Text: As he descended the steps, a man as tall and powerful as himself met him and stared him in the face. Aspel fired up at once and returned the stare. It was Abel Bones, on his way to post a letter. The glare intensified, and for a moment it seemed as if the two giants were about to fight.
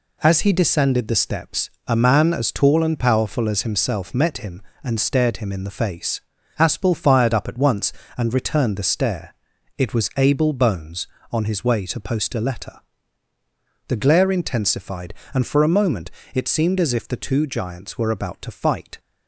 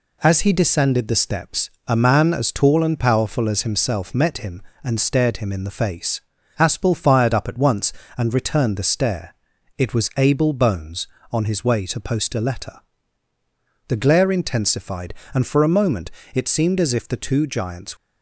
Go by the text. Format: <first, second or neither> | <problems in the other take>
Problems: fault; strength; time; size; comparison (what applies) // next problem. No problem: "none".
first | pauses between "moment" and "it"; slight; at 16.1 s; 0.22 s long; slight in the first // stops before "were about to fight"; at 17.9 s